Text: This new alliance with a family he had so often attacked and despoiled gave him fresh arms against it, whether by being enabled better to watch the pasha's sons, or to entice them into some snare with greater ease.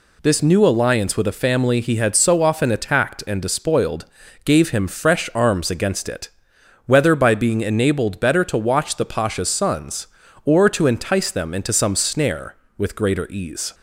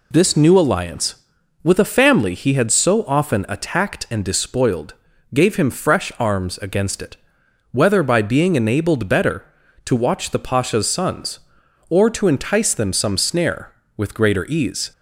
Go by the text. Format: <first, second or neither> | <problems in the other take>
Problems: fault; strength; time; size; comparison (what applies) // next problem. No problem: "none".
first | pauses between "despoiled" and "gave"; at 4.9 s; 0.40 s long; also in the first // skips "into"; at 12.9 s